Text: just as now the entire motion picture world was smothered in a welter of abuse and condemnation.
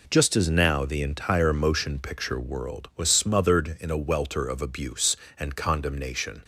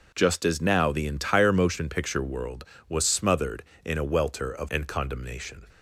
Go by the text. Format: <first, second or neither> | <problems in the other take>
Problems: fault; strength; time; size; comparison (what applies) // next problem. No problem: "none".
first | skips "abuse"; at 4.6 s